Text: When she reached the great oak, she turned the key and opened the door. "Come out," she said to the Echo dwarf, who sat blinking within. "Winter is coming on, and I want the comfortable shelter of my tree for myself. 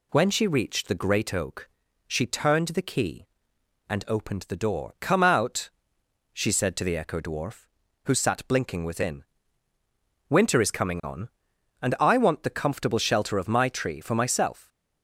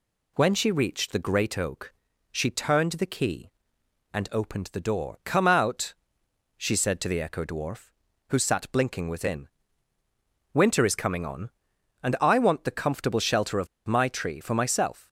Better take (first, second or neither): first